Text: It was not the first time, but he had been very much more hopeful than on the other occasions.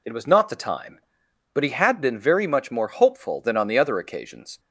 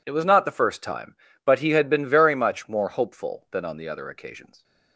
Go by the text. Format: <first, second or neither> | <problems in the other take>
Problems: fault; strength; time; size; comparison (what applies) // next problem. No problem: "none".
second | skips "first"; at 0.5 s